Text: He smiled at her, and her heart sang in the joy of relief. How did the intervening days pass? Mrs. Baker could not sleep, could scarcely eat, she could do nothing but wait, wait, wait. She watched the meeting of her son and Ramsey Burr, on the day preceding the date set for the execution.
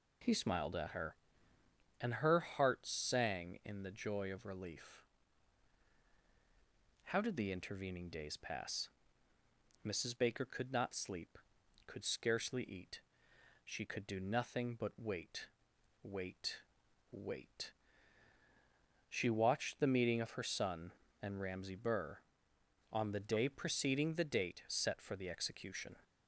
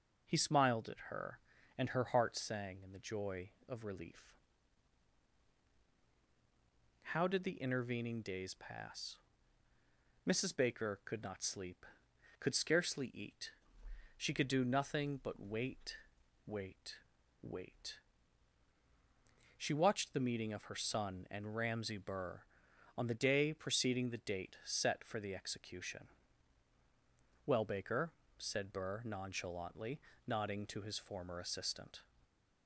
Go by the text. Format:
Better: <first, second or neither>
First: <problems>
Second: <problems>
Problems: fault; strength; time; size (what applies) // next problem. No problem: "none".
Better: first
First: none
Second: goes on to say "Well Baker said Burr nonchalantly nodding to his former assistant"; strong; from 27.4 s on; 4.5 s long